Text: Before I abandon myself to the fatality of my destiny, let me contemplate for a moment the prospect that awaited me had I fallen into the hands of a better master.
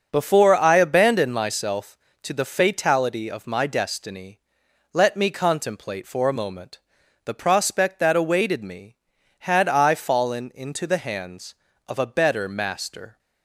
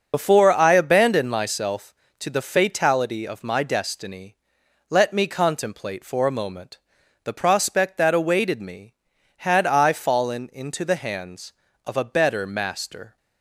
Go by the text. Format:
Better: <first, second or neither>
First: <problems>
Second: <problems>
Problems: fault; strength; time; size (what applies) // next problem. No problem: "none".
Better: first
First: starts louder than the rest; until 1.1 s; 6 dB // pauses between "moment" and "the"; noticeable; at 6.7 s; 0.46 s long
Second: loses the start of "Before"; at 0.1 s; 65 ms // starts louder than the rest; noticeable; until 1.1 s; 6 dB // pauses between "moment" and "the"; noticeable; at 6.7 s; 0.46 s long